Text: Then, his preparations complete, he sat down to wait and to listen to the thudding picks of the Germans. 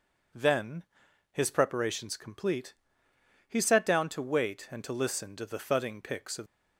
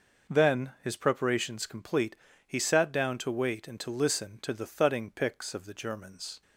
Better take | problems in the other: second | stops before "the Germans"; at 6.4 s

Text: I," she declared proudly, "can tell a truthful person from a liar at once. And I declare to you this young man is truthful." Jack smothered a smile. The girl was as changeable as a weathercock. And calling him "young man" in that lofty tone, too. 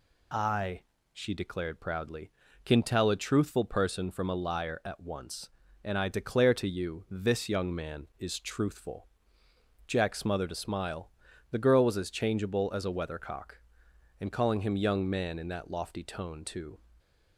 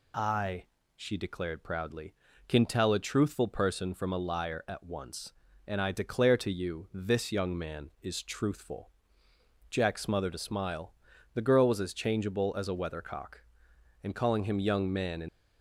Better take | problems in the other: first | stops before "that lofty tone too"; at 15.2 s

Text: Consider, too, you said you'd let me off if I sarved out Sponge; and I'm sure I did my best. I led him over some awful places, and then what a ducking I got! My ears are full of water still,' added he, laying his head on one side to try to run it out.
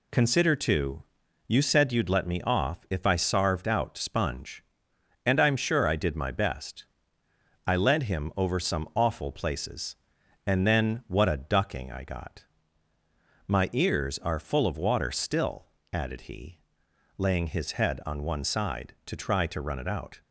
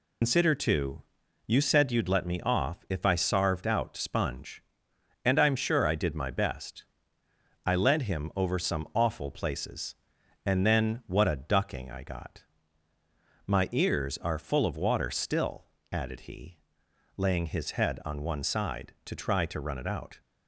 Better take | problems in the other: first | loses the start of "Consider"; at 0.2 s; 110 ms

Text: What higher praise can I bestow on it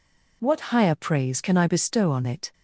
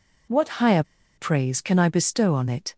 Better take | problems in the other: first | pauses between "higher" and "praise"; slight; at 0.8 s; 0.33 s long

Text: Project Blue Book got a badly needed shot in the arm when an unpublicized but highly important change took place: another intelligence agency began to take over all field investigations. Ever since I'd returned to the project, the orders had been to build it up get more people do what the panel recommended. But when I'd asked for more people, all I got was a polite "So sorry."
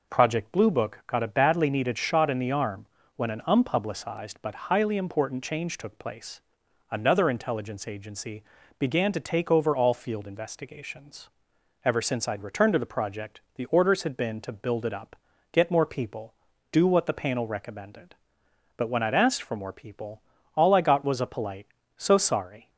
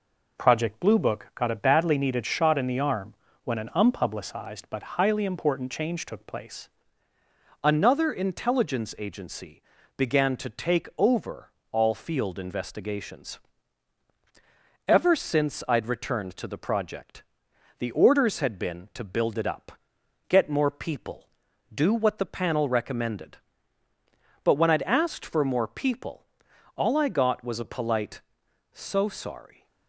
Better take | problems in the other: first | pauses between "arm" and "when"; slight; at 3.1 s; 0.30 s long; slight in the first // changes voice at "another"; from 7.6 s on; 22.0 s long // pauses between "agency" and "began"; slight; at 9.6 s; 0.34 s long; slight in the first // pauses between "over" and "all"; slight; at 11.5 s; 0.18 s long // pauses between "up" and "get"; noticeable; at 19.7 s; 0.56 s long; slight in the first

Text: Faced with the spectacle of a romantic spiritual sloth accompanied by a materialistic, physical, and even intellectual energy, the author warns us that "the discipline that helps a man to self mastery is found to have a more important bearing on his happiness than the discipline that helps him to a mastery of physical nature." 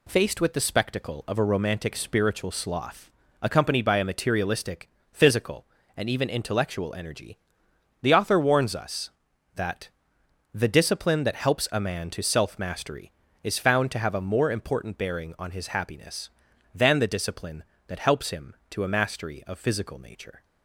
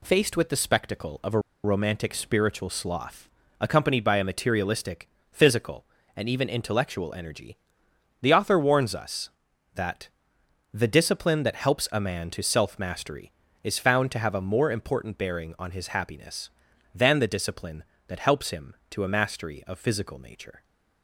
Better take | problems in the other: first | pauses between "a" and "romantic"; slight; at 1.3 s; 0.24 s long // pauses between "sloth" and "accompanied"; slight; at 3.2 s; 0.30 s long; slight in the first // pauses between "that" and "the"; noticeable; at 10.0 s; 0.66 s long; noticeable in the first

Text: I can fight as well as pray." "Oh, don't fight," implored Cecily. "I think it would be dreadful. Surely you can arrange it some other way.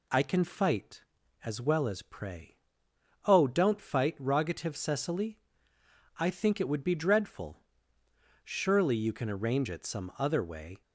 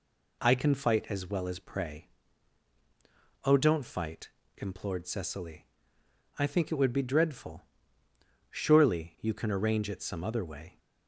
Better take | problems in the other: second | says "rogative" for "implored"; at 4.1 s

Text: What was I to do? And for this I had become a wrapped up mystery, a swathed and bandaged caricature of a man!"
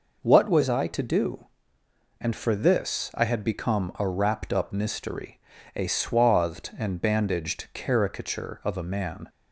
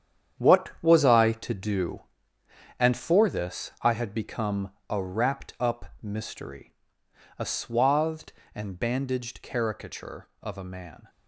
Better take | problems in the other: first | gets quieter; strong; throughout; 11 dB // pauses between "become" and "a"; slight; at 4.7 s; 0.18 s long

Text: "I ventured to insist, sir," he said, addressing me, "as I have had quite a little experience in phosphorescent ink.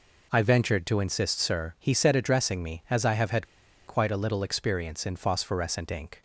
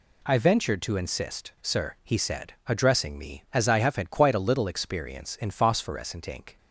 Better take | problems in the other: second | pauses between "had" and "quite"; at 3.4 s; 0.42 s long

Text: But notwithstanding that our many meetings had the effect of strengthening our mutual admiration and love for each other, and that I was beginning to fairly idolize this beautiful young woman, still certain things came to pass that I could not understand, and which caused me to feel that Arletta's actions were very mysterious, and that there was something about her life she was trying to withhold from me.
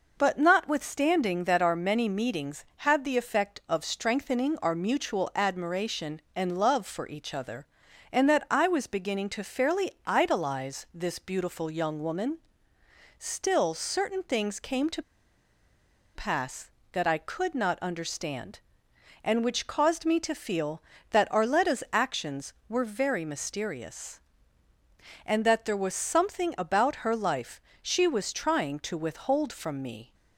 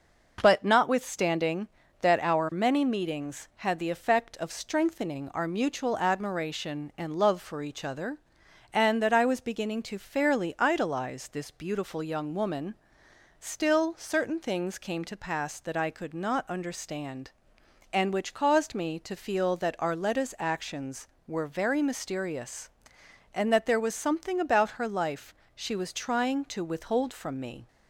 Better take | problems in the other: second | pauses between "fairly" and "idolize"; slight; at 9.9 s; 0.16 s long // pauses between "to" and "pass"; at 15.0 s; 1.1 s long // pauses between "life" and "she"; slight; at 27.5 s; 0.22 s long; slight in the second

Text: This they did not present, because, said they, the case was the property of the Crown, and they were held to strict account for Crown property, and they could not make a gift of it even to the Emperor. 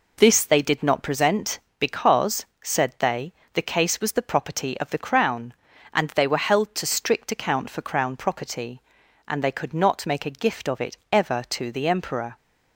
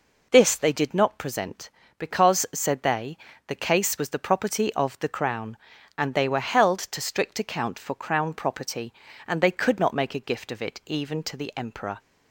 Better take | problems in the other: second | says "ever" for "even"; at 11.1 s

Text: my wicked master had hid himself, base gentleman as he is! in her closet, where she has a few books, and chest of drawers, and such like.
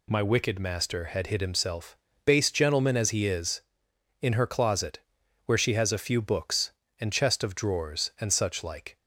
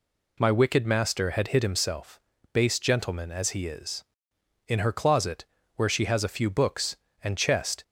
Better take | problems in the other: first | stops before "of drawers and such like"; at 7.8 s

